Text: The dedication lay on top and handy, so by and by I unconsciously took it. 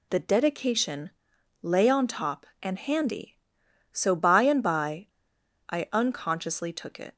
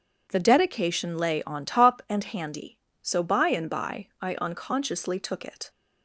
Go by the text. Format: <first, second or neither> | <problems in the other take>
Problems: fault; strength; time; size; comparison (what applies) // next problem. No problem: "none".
second | pauses between "dedication" and "lay"; noticeable; at 1.1 s; 0.52 s long // pauses between "by" and "I"; noticeable; at 5.0 s; 0.61 s long